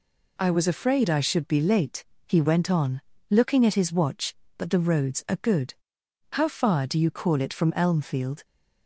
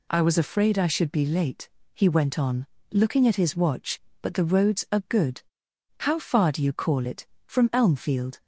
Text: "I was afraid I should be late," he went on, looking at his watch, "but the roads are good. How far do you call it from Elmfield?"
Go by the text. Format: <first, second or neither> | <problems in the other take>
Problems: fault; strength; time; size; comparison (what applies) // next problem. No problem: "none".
neither | none